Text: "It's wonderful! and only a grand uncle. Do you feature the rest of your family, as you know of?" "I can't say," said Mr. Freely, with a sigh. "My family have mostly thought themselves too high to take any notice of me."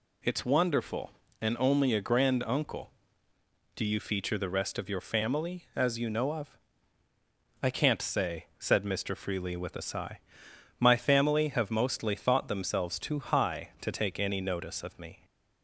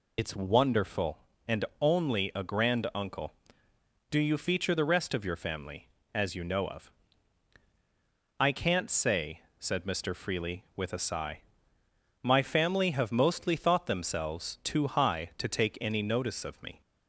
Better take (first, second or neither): first